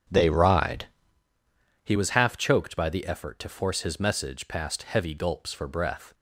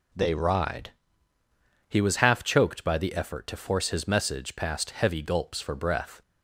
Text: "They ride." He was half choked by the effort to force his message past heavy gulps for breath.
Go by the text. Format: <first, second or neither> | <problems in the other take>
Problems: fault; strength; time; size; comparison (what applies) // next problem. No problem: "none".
second | starts louder than the rest; strong; until 1.2 s; 7.5 dB